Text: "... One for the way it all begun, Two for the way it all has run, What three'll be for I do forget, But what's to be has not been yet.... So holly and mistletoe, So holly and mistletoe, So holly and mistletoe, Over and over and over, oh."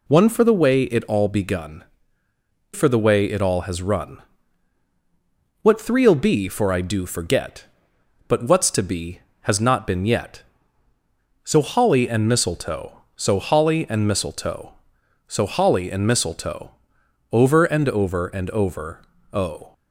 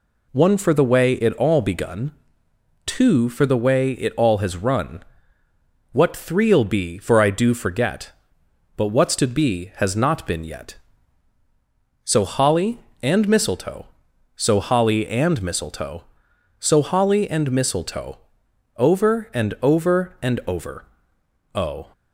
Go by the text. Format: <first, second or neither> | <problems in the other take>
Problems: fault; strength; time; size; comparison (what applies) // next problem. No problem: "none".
second | skips "Two"; at 2.2 s